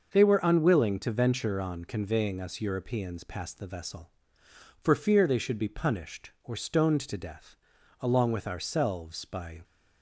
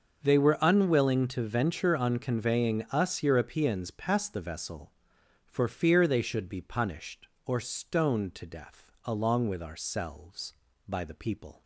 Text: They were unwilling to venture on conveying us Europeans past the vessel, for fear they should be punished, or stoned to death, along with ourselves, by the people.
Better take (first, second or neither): second